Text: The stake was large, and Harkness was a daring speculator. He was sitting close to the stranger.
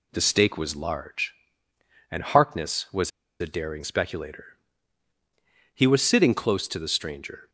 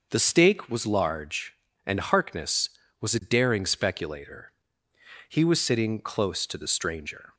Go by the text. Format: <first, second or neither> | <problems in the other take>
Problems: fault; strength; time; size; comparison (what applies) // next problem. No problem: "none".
second | pauses between "was" and "a"; slight; at 3.1 s; 0.31 s long